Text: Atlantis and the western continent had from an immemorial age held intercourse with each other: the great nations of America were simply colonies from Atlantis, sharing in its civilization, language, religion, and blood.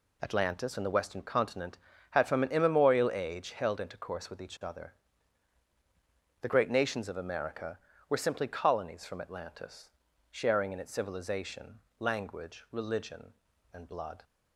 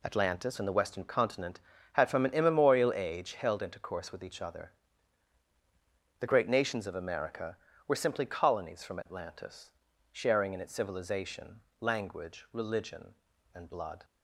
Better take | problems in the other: neither | none

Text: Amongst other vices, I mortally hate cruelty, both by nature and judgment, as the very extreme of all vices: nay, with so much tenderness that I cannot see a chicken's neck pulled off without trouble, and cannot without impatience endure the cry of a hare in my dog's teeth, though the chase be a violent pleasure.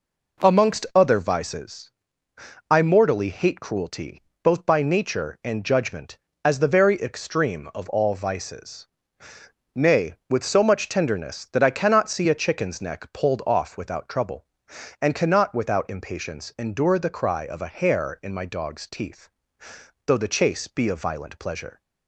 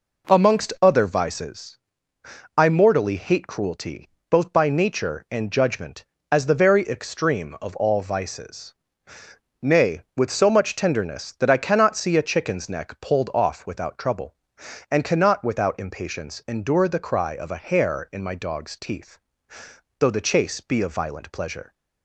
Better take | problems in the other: neither | none

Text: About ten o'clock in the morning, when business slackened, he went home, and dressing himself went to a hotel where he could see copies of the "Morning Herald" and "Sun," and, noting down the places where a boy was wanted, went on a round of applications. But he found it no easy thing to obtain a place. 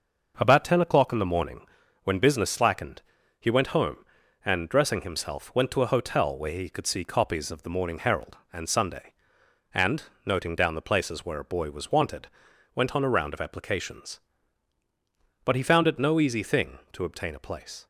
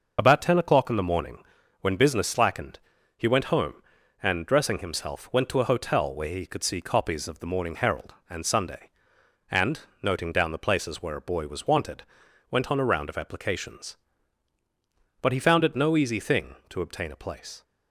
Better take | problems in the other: first | loses the start of "About"; at 0.1 s; 55 ms

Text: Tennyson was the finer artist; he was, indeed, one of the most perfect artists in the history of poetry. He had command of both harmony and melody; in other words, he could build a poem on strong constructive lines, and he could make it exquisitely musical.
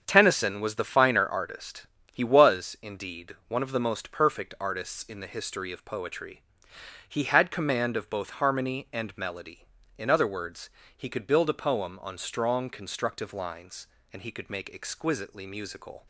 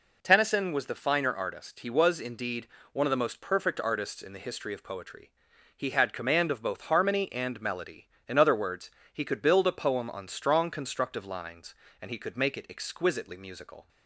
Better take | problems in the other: second | starts louder than the rest; strong; until 1.0 s; 7.5 dB // skips "it"; at 14.7 s

